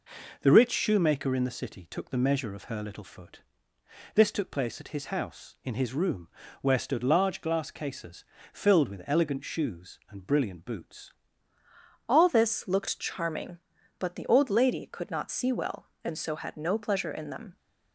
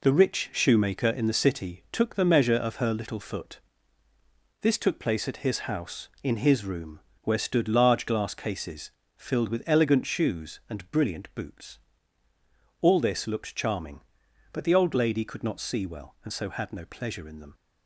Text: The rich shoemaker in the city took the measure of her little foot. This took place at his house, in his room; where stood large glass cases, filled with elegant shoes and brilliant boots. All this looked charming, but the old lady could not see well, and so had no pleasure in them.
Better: second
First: changes voice at "All"; from 12.0 s on; 5.5 s long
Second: none

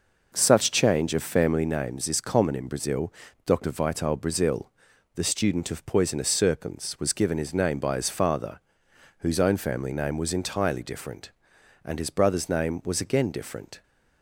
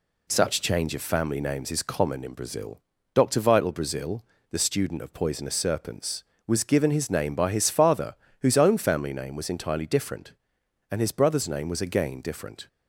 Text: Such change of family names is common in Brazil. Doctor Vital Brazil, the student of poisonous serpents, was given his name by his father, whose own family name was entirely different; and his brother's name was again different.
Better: second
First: starts louder than the rest; noticeable; until 1.7 s; 5.5 dB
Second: none

